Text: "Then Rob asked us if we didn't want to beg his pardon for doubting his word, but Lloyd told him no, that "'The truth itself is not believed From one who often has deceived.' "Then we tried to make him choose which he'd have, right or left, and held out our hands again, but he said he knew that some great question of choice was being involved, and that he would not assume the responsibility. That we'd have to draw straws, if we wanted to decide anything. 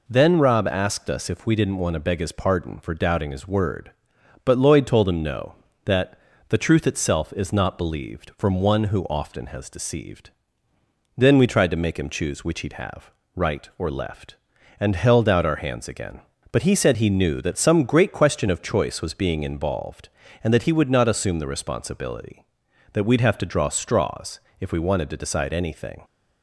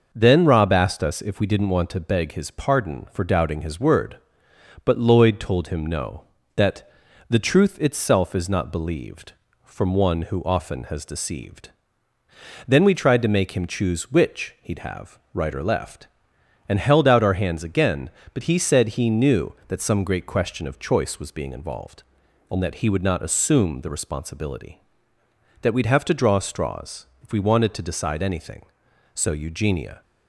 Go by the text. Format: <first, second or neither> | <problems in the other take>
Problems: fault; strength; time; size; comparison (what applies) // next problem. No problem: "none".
first | pauses between "that" and "The"; at 6.8 s; 0.40 s long; slight in the first // goes on to say "So Eugenia"; noticeable; from 29.1 s on; 0.88 s long